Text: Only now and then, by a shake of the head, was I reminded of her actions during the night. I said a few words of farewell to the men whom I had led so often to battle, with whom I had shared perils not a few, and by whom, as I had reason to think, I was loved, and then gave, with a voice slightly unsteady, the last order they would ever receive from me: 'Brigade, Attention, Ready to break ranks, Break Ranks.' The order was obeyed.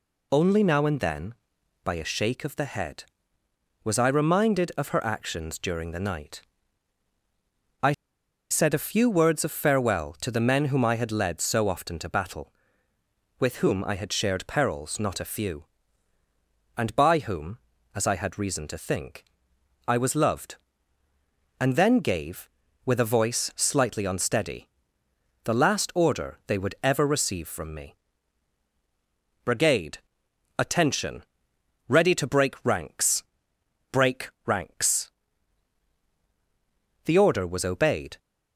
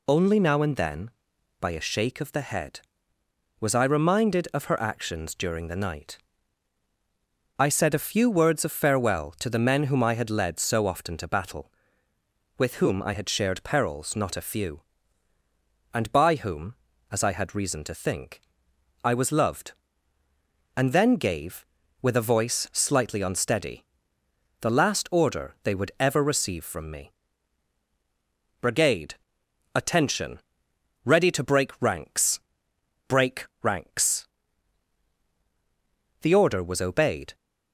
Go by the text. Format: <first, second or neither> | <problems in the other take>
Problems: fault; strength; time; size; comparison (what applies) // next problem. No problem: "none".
second | pauses between "I" and "said"; noticeable; at 7.9 s; 0.58 s long // pauses between "Break" and "Ranks"; slight; at 34.2 s; 0.16 s long; slight in the second